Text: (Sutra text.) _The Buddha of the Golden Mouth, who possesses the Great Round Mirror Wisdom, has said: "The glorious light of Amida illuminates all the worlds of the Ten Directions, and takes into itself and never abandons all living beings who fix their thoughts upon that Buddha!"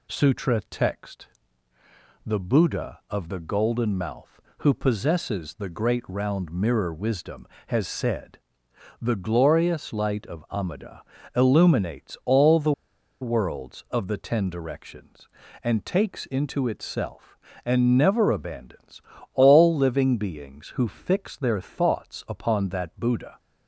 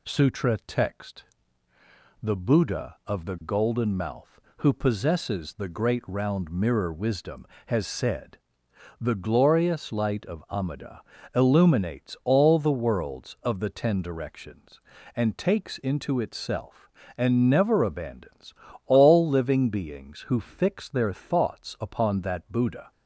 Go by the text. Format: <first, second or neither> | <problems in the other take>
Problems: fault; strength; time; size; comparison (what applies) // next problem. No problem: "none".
second | pauses between "Amida" and "illuminates"; slight; at 11.0 s; 0.34 s long; slight in the second // pauses between "the" and "worlds"; noticeable; at 12.7 s; 0.49 s long // pauses between "abandons" and "all"; slight; at 19.0 s; 0.32 s long; slight in the second